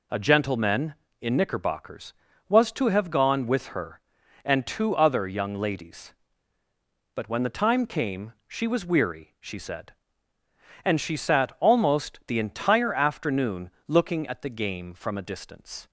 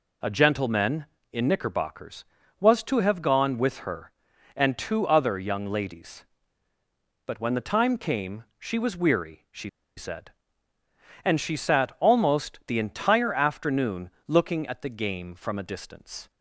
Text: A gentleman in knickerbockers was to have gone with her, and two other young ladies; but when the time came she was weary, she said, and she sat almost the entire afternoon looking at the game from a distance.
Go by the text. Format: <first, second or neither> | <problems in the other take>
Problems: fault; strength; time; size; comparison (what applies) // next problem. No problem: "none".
first | pauses between "came" and "she"; slight; at 8.4 s; 0.16 s long; slight in the first // pauses between "she" and "said"; slight; at 9.6 s; 0.28 s long // pauses between "afternoon" and "looking"; slight; at 14.0 s; 0.18 s long; slight in the first